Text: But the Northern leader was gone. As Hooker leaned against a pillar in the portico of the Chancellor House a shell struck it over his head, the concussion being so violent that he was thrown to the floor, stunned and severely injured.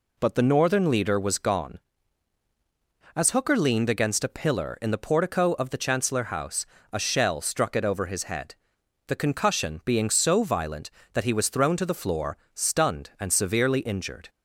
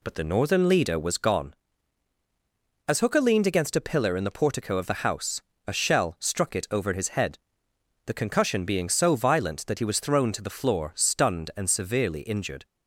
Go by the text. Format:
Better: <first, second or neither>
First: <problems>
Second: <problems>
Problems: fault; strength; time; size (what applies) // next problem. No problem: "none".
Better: first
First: pauses between "House" and "a"; slight; at 6.6 s; 0.26 s long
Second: skips "Chancellor"; at 5.0 s // pauses between "House" and "a"; slight; at 5.4 s; 0.24 s long